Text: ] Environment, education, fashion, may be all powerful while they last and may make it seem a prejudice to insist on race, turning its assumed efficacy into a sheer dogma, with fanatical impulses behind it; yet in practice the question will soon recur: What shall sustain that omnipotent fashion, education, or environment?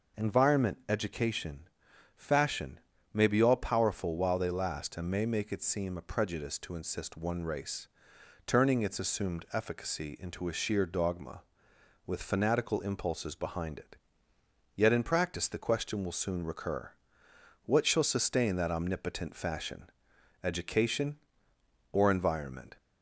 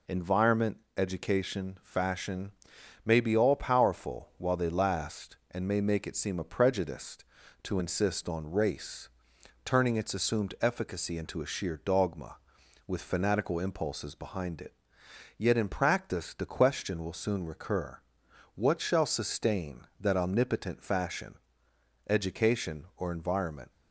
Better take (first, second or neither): second